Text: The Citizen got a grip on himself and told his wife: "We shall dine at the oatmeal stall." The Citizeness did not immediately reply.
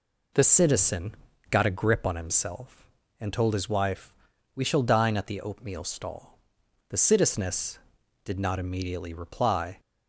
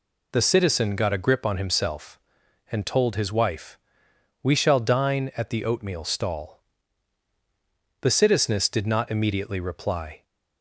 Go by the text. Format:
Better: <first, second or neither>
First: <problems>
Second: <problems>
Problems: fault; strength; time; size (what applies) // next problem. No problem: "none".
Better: second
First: changes voice at "Citizen"; from 0.4 s on; 9.3 s long // pauses between "Citizen" and "got"; slight; at 1.1 s; 0.36 s long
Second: none